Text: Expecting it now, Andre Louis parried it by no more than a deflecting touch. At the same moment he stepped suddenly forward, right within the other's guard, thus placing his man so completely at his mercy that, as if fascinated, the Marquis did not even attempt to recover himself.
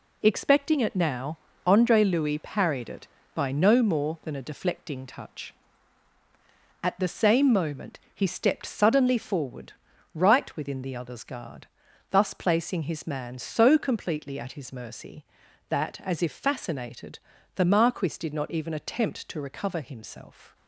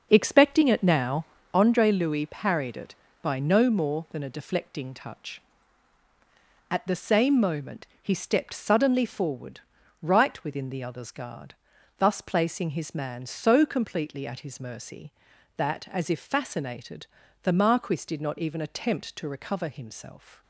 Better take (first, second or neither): first